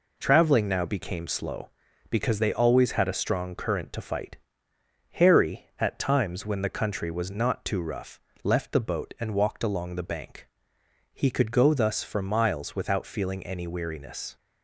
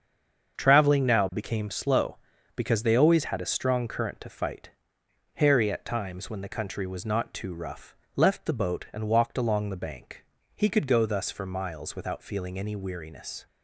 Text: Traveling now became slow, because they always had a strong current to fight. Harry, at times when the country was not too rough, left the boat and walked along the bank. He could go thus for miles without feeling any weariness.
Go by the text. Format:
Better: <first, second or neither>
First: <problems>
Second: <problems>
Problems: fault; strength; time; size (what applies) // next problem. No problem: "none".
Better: first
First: none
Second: stays silent before the first word; slight; until 0.5 s; 0.5 s long // starts louder than the rest; until 1.6 s; 7 dB